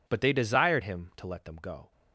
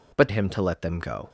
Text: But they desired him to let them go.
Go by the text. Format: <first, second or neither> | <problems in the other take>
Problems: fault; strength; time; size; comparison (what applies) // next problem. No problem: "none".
first | skips "they desired"; at 0.2 s